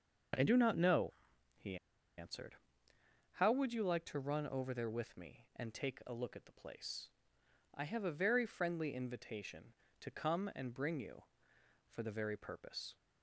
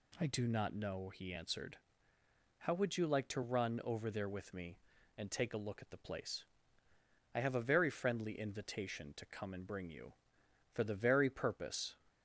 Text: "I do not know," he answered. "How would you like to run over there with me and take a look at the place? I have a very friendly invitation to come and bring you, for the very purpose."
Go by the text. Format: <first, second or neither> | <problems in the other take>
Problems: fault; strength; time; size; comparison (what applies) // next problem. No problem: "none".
second | starts louder than the rest; until 2.2 s; 6.5 dB // pauses between "he" and "answered"; at 1.7 s; 0.41 s long